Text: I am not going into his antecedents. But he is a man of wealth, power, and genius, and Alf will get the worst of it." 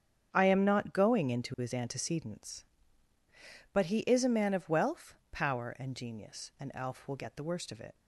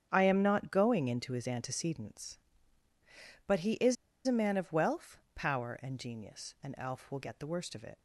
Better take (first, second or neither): first